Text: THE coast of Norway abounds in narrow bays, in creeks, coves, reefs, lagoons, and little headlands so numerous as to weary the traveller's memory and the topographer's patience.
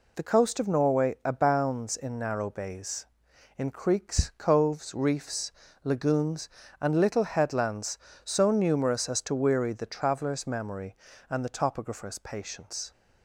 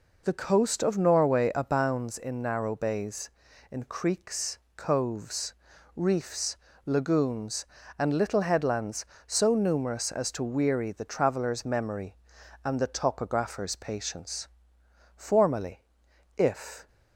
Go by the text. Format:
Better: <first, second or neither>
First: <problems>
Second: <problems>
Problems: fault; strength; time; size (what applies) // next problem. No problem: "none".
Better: first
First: none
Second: goes on to say "Formerly if"; strong; from 15.1 s on; 1.7 s long